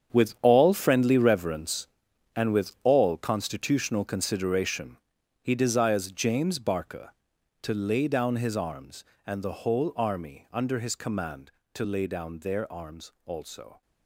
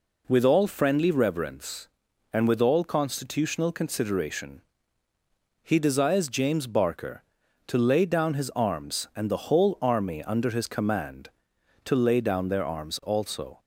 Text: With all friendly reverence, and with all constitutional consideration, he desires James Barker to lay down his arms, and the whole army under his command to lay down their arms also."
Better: second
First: gets quieter; strong; throughout; 13 dB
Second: none

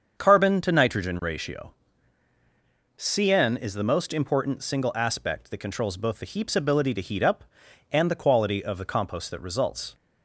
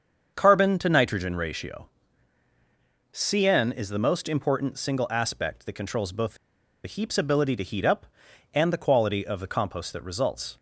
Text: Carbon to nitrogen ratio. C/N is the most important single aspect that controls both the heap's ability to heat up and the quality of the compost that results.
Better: first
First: starts louder than the rest; until 1.1 s; 7 dB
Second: starts louder than the rest; until 1.3 s; 7 dB // pauses between "the" and "heap's"; noticeable; at 6.3 s; 0.49 s long

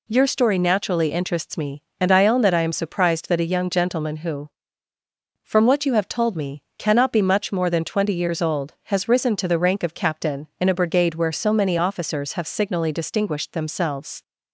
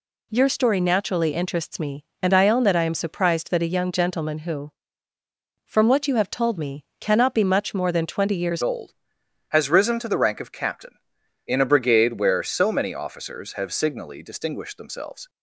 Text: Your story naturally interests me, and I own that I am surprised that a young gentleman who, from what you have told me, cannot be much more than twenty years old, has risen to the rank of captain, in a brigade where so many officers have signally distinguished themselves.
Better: first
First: none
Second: changes voice at "old"; from 8.6 s on; 6.6 s long

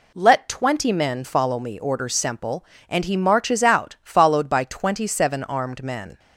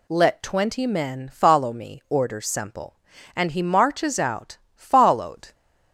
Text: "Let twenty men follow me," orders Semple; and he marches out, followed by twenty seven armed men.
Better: first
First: none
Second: stops before "by twenty seven armed men"; at 5.5 s

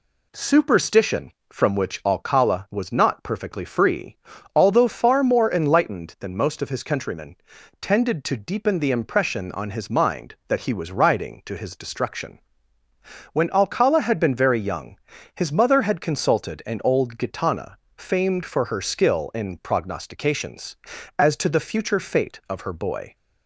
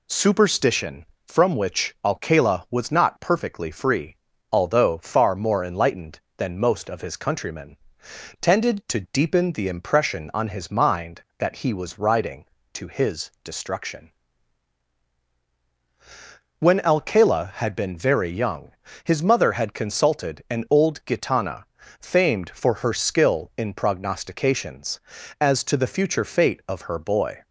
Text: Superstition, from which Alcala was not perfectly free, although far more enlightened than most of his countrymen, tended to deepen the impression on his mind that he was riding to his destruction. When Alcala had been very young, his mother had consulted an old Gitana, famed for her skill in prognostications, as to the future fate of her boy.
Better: neither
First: none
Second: none

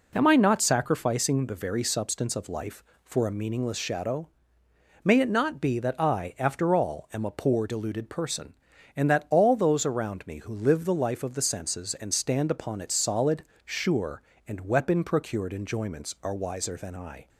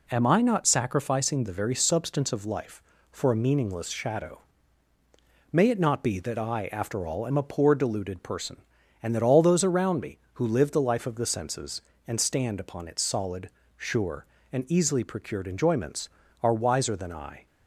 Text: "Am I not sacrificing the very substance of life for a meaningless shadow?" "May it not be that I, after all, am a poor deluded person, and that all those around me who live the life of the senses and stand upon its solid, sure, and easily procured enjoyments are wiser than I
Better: second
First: says "weapon" for "easily"; at 14.6 s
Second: none

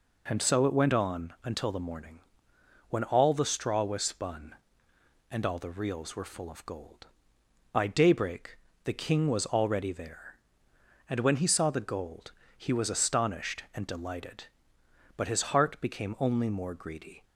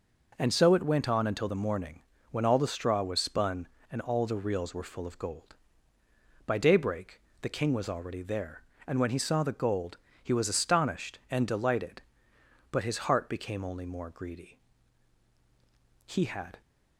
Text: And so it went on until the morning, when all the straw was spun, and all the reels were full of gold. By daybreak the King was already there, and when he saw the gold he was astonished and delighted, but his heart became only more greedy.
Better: first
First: pauses between "daybreak" and "the"; slight; at 8.5 s; 0.28 s long // pauses between "gold" and "he"; slight; at 12.3 s; 0.25 s long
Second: pauses between "daybreak" and "the"; slight; at 7.1 s; 0.22 s long // pauses between "gold" and "he"; slight; at 9.9 s; 0.26 s long // goes on to say "He had"; from 16.0 s on; 0.54 s long

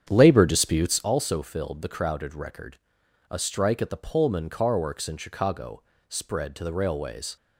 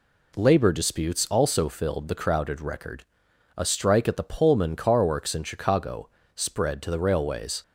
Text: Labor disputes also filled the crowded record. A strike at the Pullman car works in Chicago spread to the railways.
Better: second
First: starts louder than the rest; strong; until 1.1 s; 8.5 dB // pauses between "Chicago" and "spread"; slight; at 5.8 s; 0.26 s long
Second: pauses between "Chicago" and "spread"; slight; at 6.0 s; 0.26 s long

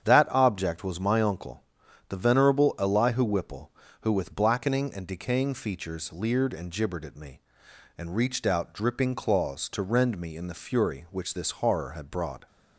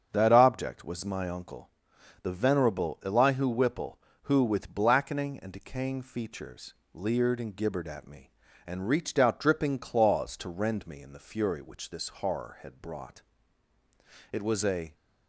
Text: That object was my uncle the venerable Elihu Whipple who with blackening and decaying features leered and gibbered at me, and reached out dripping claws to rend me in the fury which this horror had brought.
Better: first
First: starts louder than the rest; strong; until 1.0 s; 8 dB // pauses between "uncle" and "the"; noticeable; at 1.6 s; 0.46 s long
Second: starts louder than the rest; strong; until 1.1 s; 8 dB // pauses between "uncle" and "the"; noticeable; at 1.6 s; 0.52 s long // pauses between "features" and "leered"; slight; at 6.7 s; 0.18 s long // goes on to say "It was a"; noticeable; from 14.3 s on; 0.62 s long

